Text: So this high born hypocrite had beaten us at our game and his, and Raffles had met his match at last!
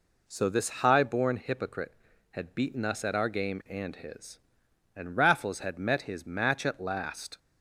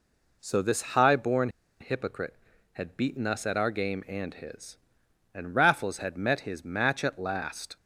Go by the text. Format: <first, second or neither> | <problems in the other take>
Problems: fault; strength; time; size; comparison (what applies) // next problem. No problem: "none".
first | pauses between "born" and "hypocrite"; slight; at 1.4 s; 0.31 s long